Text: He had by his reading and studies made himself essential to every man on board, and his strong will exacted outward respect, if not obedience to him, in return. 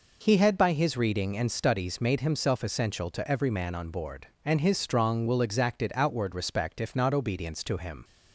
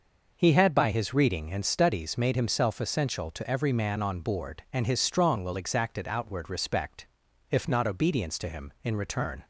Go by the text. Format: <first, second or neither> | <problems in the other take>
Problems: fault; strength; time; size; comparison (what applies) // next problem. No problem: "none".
second | stops before "in return"; at 8.0 s